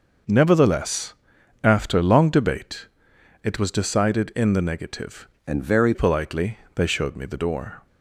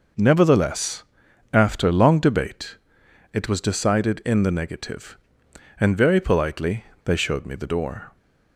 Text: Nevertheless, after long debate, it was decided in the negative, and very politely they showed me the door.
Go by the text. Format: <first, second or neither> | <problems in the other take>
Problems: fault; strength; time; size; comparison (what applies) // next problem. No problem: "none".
second | changes voice from "and" to "very"; from 5.4 to 5.9 s; 0.5 s long // pauses between "politely" and "they"; slight; at 6.5 s; 0.16 s long; slight in the second